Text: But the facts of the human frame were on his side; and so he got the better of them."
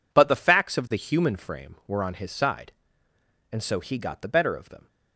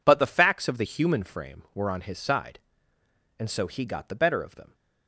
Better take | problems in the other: neither | none

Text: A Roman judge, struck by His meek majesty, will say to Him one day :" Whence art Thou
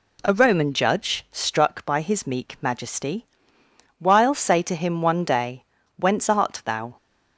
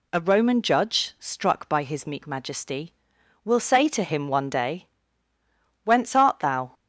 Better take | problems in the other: second | says "while" for "will"; at 3.9 s

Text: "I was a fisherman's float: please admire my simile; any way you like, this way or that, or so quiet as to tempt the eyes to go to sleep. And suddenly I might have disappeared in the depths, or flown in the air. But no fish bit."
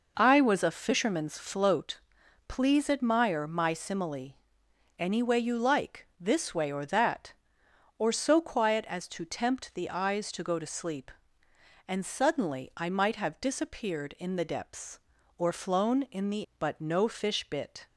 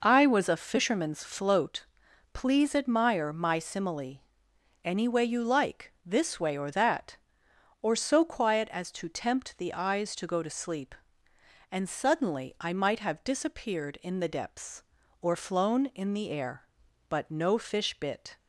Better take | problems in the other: second | skips "air"; at 16.5 s

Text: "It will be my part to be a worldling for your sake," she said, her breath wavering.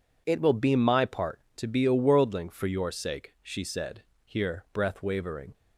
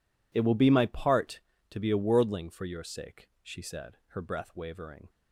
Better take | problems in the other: second | says "here" for "her"; at 4.2 s

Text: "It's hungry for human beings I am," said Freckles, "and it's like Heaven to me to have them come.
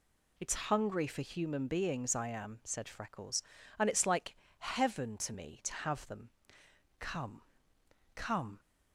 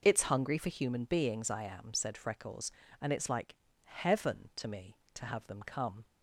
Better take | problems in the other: second | pauses between "like" and "Heaven"; slight; at 4.3 s; 0.22 s long; slight in the second // pauses between "them" and "come"; noticeable; at 6.2 s; 0.72 s long // says "come" twice; at 8.1 s

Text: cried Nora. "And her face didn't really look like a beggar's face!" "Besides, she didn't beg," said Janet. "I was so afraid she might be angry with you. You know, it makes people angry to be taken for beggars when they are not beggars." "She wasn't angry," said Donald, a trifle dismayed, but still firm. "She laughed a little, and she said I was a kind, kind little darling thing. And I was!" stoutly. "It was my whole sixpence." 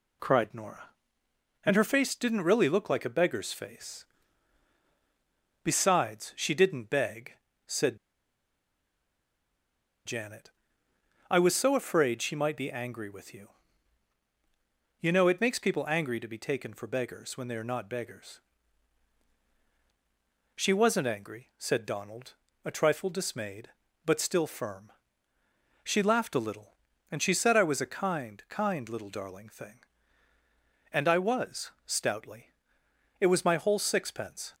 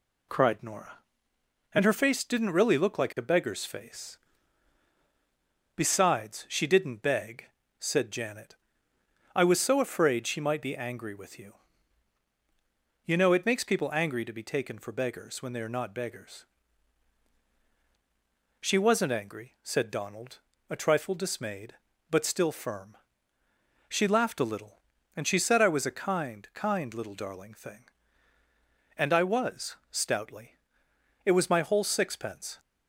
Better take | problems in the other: second | pauses between "said" and "Janet"; strong; at 7.9 s; 2.0 s long

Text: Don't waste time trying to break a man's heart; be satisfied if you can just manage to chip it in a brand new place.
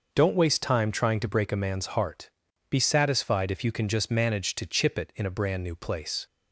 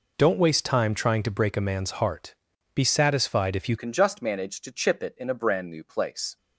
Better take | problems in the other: first | changes voice at "can"; from 3.7 s on; 2.6 s long

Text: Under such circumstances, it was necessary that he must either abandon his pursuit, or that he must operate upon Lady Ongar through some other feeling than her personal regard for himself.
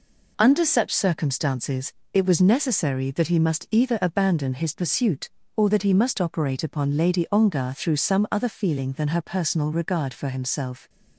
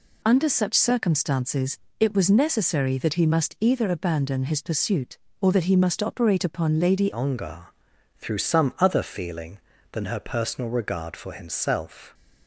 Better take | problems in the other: first | changes voice at "Ongar"; from 7.1 s on; 5.0 s long // pauses between "Ongar" and "through"; noticeable; at 7.6 s; 0.50 s long

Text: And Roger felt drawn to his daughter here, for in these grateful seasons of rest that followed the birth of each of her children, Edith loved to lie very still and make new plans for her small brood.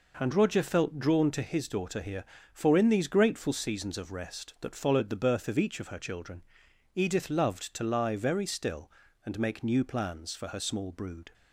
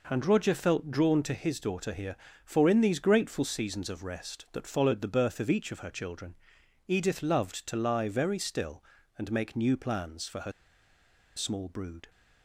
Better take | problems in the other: first | pauses between "her" and "small"; noticeable; at 10.5 s; 0.84 s long

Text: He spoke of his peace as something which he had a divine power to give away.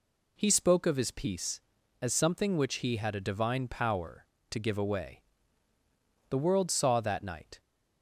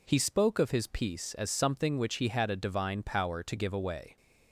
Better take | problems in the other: second | goes on to say "The world saw that night"; from 6.2 s on; 1.3 s long

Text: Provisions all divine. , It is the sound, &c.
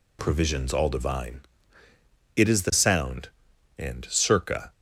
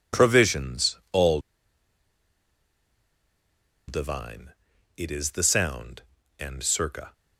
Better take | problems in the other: first | pauses between "all" and "divine"; strong; at 1.3 s; 2.4 s long

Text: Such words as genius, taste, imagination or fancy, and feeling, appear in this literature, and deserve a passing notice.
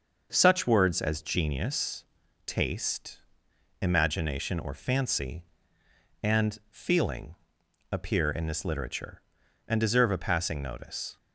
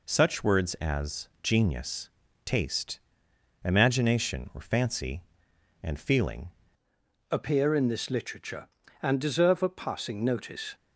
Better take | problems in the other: first | pauses between "as" and "genius"; slight; at 1.2 s; 0.16 s long // changes voice at "appear"; from 7.3 s on; 3.4 s long

